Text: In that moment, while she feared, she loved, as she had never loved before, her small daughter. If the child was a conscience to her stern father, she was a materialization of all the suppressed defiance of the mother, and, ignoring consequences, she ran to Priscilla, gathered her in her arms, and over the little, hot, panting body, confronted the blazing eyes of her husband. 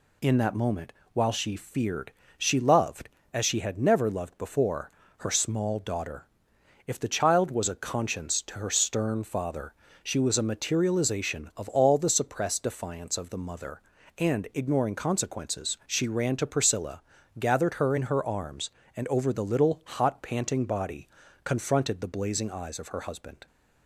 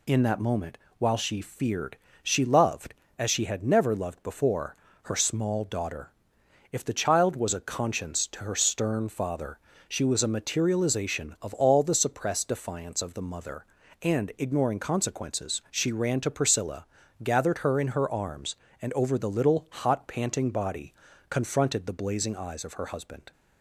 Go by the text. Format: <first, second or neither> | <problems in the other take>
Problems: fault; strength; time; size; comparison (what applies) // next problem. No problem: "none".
neither | none